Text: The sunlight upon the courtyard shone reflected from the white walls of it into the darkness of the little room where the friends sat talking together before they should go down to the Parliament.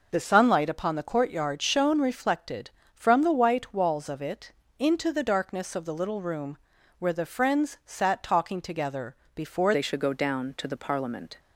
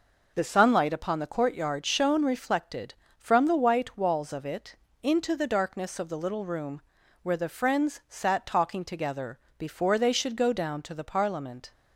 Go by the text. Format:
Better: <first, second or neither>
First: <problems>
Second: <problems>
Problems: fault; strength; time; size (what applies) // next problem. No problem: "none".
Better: second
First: pauses between "it" and "into"; slight; at 4.5 s; 0.26 s long // pauses between "room" and "where"; at 6.5 s; 0.42 s long // pauses between "together" and "before"; slight; at 9.1 s; 0.18 s long // changes voice at "they"; from 9.7 s on; 1.6 s long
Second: pauses between "it" and "into"; slight; at 4.7 s; 0.26 s long // pauses between "room" and "where"; at 6.8 s; 0.42 s long // pauses between "together" and "before"; slight; at 9.3 s; 0.18 s long